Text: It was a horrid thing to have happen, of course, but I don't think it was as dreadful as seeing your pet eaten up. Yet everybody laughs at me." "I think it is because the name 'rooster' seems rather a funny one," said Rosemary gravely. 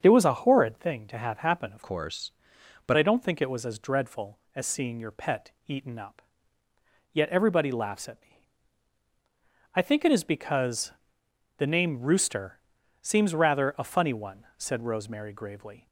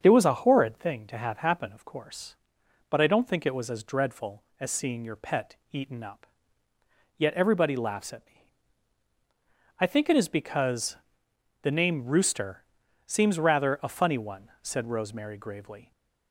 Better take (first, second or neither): second